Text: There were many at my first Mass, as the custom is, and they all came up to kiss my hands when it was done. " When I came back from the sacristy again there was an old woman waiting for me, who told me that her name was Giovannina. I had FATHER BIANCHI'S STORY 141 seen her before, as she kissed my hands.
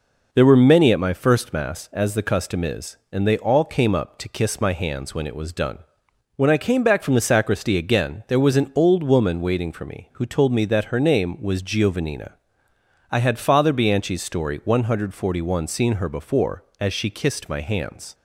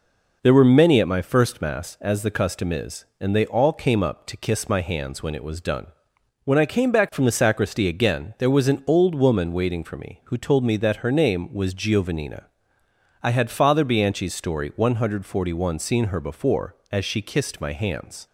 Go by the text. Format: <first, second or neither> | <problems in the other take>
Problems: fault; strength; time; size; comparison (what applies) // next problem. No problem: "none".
neither | none